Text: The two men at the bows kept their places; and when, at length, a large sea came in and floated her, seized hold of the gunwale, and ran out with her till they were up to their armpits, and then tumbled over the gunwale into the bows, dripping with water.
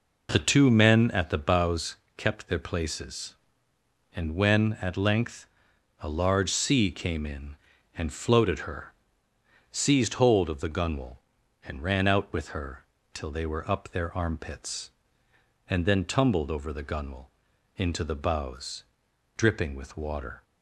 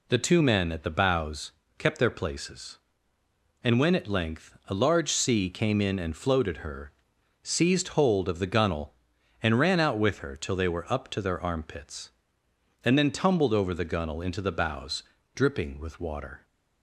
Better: second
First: pauses between "bows" and "kept"; slight; at 1.9 s; 0.20 s long // pauses between "her" and "till"; slight; at 12.8 s; 0.30 s long // skips "to"; at 13.8 s // pauses between "gunwale" and "into"; noticeable; at 17.3 s; 0.46 s long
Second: pauses between "bows" and "kept"; slight; at 1.5 s; 0.28 s long

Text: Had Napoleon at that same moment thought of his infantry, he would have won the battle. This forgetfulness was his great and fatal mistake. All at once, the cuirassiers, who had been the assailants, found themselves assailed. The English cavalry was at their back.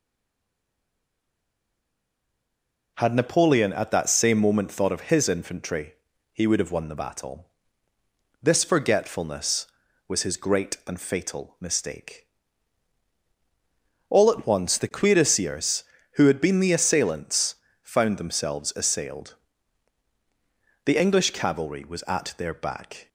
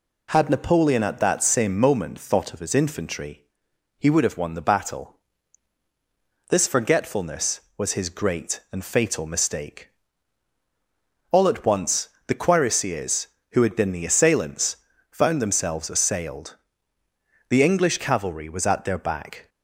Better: second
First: stays silent before the first word; strong; until 2.9 s; 2.9 s long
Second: none

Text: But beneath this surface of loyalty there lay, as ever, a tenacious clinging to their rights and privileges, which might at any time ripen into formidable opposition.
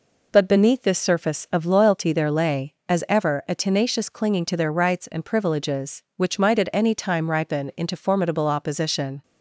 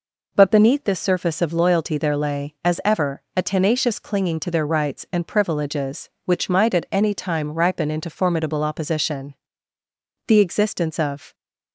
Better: first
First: none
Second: goes on to say "The existence of"; noticeable; from 10.2 s on; 1.0 s long

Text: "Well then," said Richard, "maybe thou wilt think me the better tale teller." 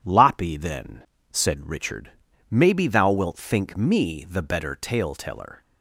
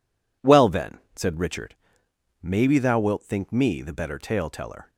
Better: second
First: says "Loppy" for "Well"; at 0.0 s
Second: none

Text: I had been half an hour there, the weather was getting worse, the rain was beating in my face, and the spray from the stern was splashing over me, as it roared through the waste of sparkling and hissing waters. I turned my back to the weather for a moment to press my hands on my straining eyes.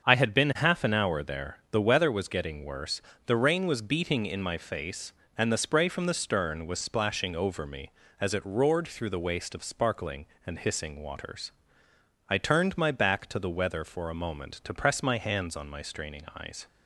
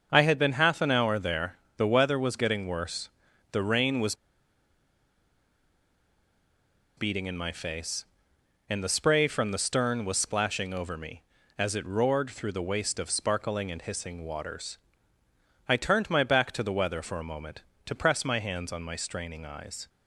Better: first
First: starts louder than the rest; until 1.1 s; 7 dB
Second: starts louder than the rest; until 1.1 s; 6.5 dB // pauses between "was" and "beating"; strong; at 4.1 s; 2.8 s long

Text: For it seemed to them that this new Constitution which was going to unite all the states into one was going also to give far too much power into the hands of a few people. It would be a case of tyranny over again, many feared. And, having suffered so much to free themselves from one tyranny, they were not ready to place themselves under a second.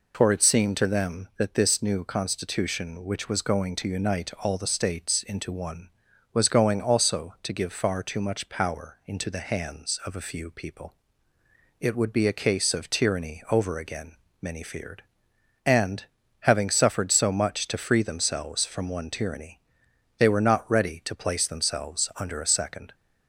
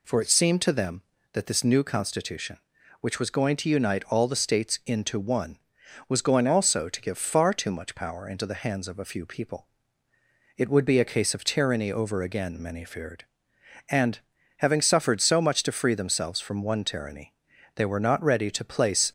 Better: first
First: none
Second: stops before "themselves under a second"; at 19.0 s

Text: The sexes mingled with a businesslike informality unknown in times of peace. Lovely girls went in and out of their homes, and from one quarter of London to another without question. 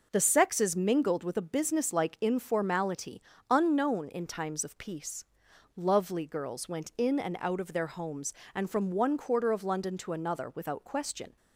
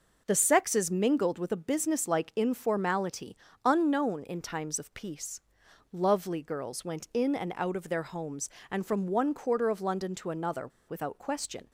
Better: first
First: pauses between "informality" and "unknown"; slight; at 3.2 s; 0.30 s long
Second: pauses between "informality" and "unknown"; slight; at 3.3 s; 0.30 s long // pauses between "another" and "without"; slight; at 10.6 s; 0.18 s long

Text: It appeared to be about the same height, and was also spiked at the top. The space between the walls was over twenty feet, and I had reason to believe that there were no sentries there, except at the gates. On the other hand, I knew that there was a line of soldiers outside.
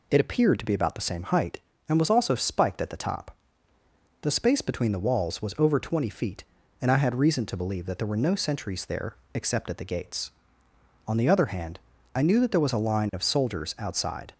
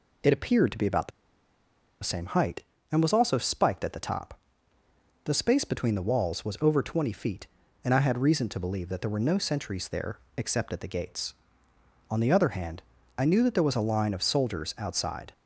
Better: first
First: none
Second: pauses between "the" and "same"; noticeable; at 1.1 s; 0.93 s long

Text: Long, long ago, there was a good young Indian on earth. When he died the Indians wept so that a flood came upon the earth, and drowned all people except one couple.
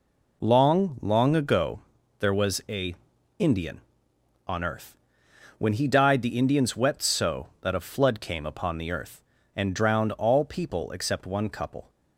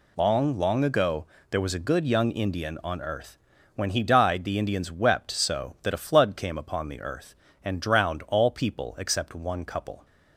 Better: second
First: skips "good young"; at 3.1 s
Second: none

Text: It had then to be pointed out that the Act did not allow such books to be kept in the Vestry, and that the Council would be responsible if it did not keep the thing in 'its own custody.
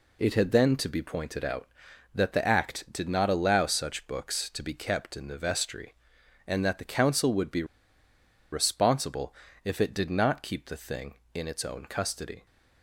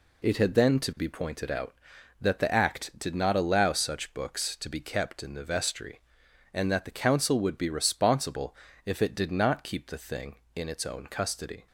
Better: second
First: pauses between "be" and "responsible"; noticeable; at 7.6 s; 0.88 s long // pauses between "responsible" and "if"; slight; at 9.3 s; 0.32 s long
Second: pauses between "responsible" and "if"; slight; at 8.5 s; 0.32 s long

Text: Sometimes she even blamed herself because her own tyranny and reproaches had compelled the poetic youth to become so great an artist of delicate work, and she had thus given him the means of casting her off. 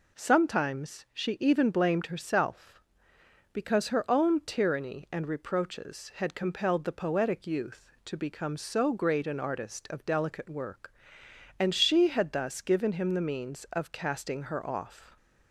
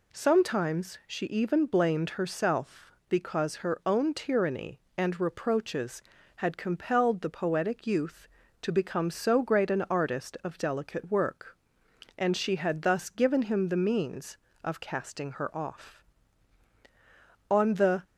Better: first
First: none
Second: goes on to say "On the"; from 17.5 s on; 0.52 s long

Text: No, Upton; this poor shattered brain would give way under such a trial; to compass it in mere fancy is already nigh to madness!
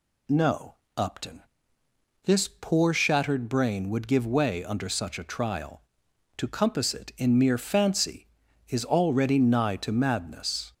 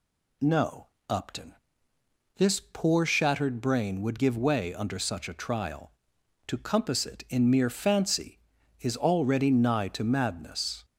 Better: neither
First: none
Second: none

